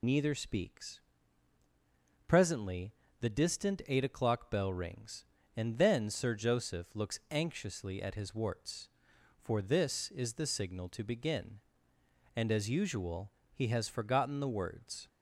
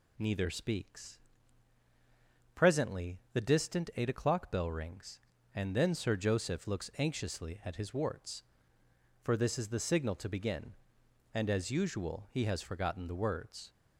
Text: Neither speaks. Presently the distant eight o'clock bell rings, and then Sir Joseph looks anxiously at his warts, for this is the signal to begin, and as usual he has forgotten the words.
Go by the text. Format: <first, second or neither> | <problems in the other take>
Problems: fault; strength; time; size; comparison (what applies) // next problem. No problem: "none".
second | loses the start of "Neither"; at 0.0 s; 60 ms // pauses between "Presently" and "the"; slight; at 2.9 s; 0.26 s long; slight in the second // pauses between "usual" and "he"; slight; at 13.3 s; 0.20 s long